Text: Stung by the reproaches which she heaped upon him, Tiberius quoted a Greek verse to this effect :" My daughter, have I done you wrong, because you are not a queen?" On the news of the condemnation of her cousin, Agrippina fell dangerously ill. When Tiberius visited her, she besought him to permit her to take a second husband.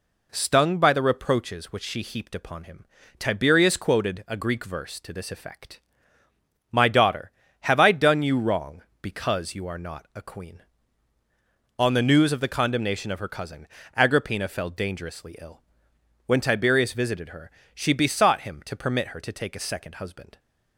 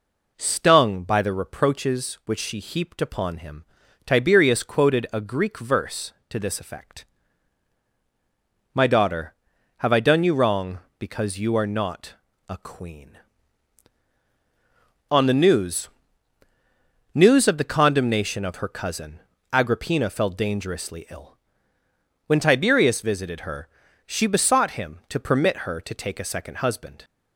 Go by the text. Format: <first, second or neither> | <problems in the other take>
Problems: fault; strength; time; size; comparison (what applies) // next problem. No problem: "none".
first | pauses between "not" and "a"; slight; at 12.1 s; 0.34 s long // says "news" twice; at 17.1 s